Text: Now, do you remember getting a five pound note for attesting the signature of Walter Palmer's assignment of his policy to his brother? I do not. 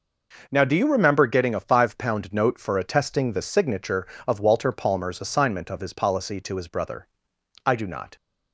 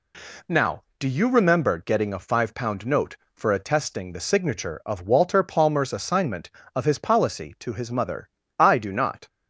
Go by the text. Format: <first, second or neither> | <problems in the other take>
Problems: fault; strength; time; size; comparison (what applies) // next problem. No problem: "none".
first | says "mother" for "brother"; at 7.9 s